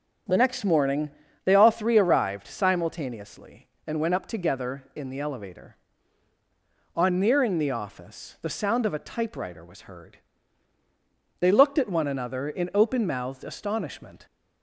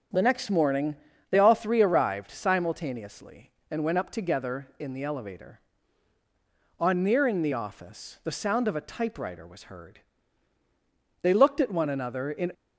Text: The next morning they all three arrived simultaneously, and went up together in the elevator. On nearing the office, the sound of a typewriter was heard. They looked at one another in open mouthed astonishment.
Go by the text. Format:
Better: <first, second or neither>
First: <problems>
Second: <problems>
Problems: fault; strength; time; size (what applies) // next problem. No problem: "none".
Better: first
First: starts louder than the rest; until 1.6 s; 6 dB // pauses between "morning" and "they"; slight; at 1.1 s; 0.32 s long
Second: starts louder than the rest; until 1.4 s; 6.5 dB // pauses between "morning" and "they"; slight; at 0.9 s; 0.32 s long // stops before "open mouthed astonishment"; at 12.5 s